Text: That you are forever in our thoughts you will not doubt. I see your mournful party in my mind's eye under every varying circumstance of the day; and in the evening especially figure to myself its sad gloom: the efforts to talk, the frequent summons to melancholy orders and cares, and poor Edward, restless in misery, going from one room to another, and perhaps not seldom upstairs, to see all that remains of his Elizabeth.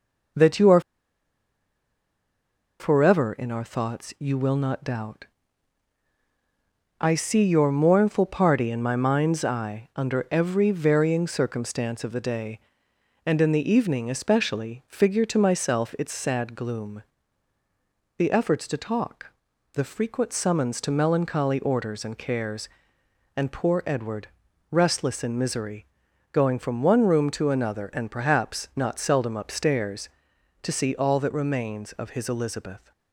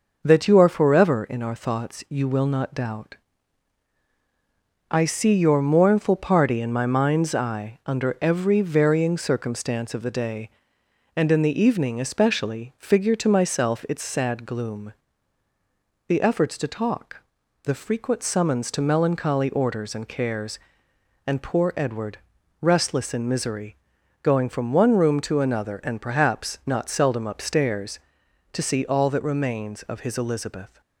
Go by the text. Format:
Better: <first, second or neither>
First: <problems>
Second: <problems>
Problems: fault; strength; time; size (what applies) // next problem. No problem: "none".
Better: second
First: pauses between "are" and "forever"; strong; at 0.8 s; 1.9 s long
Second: none